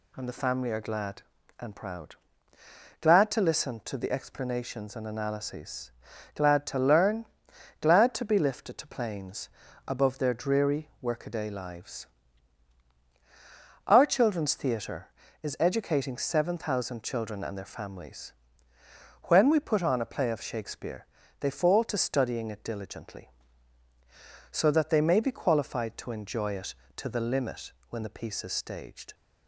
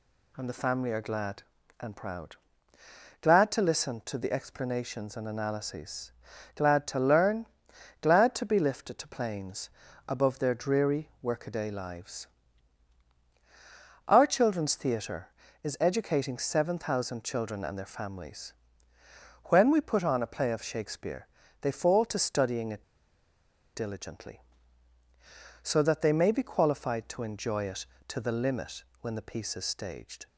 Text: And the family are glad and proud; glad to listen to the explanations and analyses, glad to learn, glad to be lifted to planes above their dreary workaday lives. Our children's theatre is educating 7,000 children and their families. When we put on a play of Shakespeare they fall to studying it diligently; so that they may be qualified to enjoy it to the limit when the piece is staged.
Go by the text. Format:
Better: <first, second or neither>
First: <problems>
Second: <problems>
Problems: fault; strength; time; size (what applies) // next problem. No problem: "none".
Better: first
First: pauses between "planes" and "above"; at 9.4 s; 0.38 s long // pauses between "Shakespeare" and "they"; slight; at 21.0 s; 0.32 s long // pauses between "limit" and "when"; slight; at 27.7 s; 0.16 s long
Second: pauses between "planes" and "above"; at 9.6 s; 0.38 s long // pauses between "Shakespeare" and "they"; slight; at 21.2 s; 0.32 s long // pauses between "it" and "diligently"; noticeable; at 22.8 s; 0.90 s long // pauses between "limit" and "when"; slight; at 28.8 s; 0.16 s long